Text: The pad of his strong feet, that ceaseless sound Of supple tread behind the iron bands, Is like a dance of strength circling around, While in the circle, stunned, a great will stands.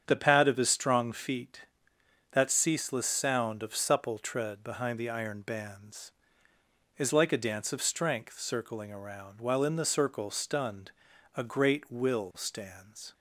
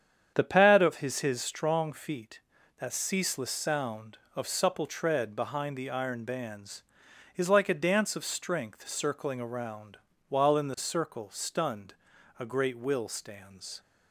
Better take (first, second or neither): first